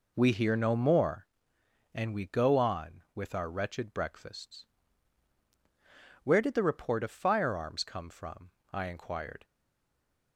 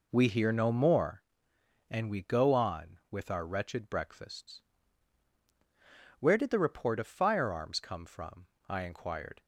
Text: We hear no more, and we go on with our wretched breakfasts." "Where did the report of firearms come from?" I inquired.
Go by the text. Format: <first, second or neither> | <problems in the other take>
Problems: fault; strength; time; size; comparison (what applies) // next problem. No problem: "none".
second | stays silent after the last word; slight; from 9.4 s on; 0.9 s long